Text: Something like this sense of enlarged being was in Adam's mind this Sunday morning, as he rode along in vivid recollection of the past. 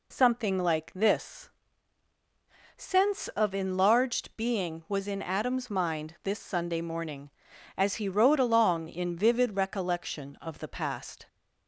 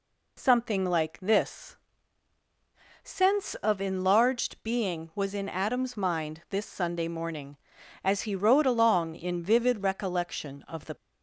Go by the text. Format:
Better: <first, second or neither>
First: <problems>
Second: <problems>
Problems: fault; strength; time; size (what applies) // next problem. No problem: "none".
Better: first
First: pauses between "this" and "sense"; strong; at 1.4 s; 1.2 s long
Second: pauses between "this" and "sense"; strong; at 1.7 s; 1.2 s long // stops before "past"; at 10.9 s